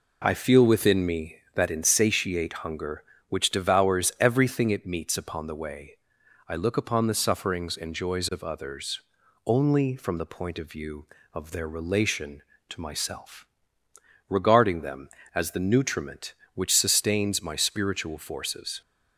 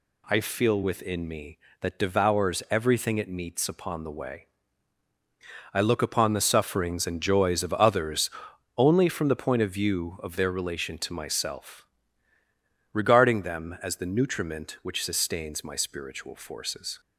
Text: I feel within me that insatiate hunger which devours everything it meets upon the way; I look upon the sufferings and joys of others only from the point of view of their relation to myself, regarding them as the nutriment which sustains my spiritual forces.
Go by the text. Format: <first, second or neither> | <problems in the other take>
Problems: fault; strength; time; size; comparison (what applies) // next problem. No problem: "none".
first | skips "insatiate hunger which"; at 1.9 s // pauses between "others" and "only"; noticeable; at 8.2 s; 0.48 s long; also in the first